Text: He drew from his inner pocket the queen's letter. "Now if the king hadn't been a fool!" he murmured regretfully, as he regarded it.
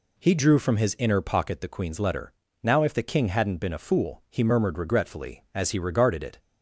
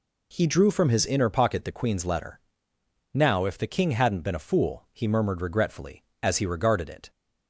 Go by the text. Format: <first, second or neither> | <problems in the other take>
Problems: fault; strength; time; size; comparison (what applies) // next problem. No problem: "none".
neither | none